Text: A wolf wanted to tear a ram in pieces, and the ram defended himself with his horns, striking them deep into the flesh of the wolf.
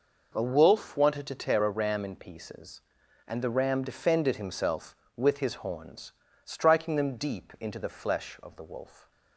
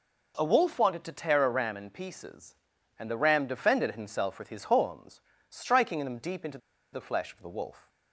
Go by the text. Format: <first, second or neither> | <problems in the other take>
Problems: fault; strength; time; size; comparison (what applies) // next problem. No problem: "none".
first | pauses between "into" and "the"; slight; at 6.5 s; 0.35 s long